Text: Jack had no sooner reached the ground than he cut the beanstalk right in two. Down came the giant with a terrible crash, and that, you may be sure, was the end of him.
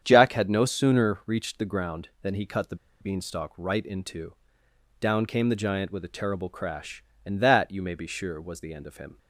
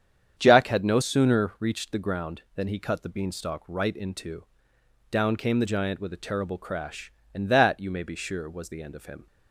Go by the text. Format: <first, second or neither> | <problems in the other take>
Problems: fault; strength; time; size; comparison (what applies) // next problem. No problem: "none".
second | starts louder than the rest; strong; until 1.0 s; 8 dB; strong in the second // pauses between "the" and "beanstalk"; slight; at 2.7 s; 0.25 s long